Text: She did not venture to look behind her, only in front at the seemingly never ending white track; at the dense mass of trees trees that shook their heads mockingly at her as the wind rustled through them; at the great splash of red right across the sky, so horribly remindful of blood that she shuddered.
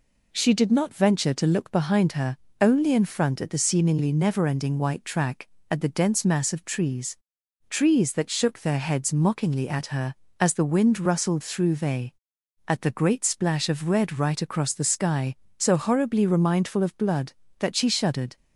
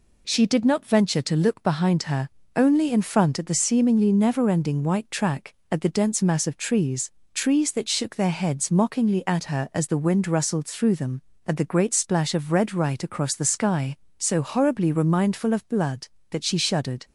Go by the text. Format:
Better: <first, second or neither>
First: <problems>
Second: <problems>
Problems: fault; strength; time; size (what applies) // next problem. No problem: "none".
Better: second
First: pauses between "trees" and "trees"; noticeable; at 7.1 s; 0.50 s long // says "they" for "them"; at 11.7 s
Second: pauses between "trees" and "trees"; slight; at 7.1 s; 0.24 s long